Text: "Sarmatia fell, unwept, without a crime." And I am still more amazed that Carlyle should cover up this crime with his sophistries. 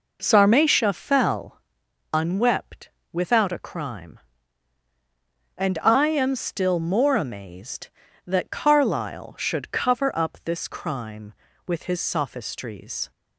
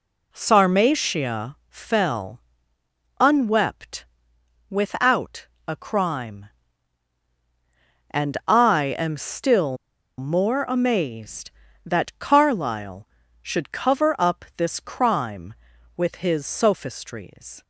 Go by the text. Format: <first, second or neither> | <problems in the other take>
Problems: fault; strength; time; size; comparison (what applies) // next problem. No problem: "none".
first | pauses between "without" and "a"; slight; at 5.4 s; 0.20 s long // pauses between "still" and "more"; at 9.7 s; 0.41 s long